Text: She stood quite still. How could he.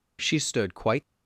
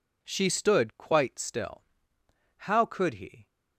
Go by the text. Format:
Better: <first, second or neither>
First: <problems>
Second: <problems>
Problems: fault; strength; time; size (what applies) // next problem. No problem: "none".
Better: second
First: stops before "still How could he"; at 1.0 s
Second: none